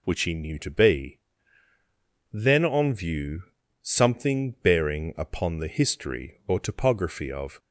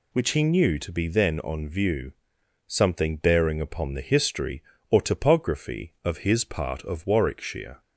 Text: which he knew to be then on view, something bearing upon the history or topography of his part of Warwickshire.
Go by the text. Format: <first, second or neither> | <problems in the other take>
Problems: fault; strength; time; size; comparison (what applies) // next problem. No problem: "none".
second | pauses between "be" and "then"; at 1.1 s; 1.1 s long // stops before "his part of Warwickshire"; at 7.5 s